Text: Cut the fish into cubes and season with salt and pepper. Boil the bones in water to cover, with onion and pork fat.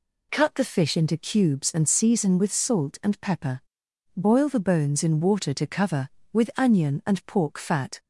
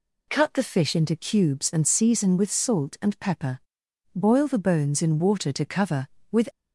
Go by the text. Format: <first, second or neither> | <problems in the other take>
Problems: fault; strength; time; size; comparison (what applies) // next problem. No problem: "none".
first | stops before "onion and pork fat"; at 6.5 s